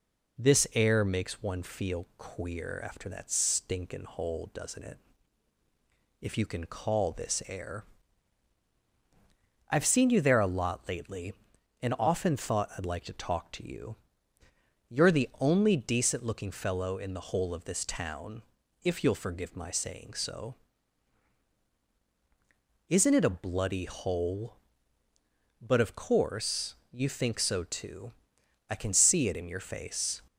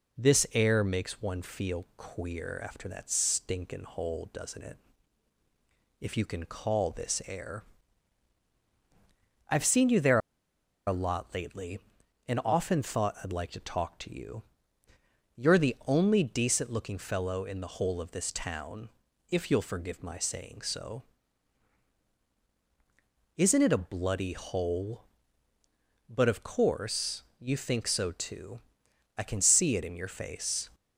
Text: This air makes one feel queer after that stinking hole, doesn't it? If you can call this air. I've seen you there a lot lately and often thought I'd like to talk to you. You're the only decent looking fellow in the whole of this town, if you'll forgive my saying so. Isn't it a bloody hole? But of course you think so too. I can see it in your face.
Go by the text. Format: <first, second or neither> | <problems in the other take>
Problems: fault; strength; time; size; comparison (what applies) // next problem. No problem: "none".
first | pauses between "there" and "a"; noticeable; at 10.1 s; 0.69 s long // pauses between "course" and "you"; slight; at 27.2 s; 0.18 s long; slight in the first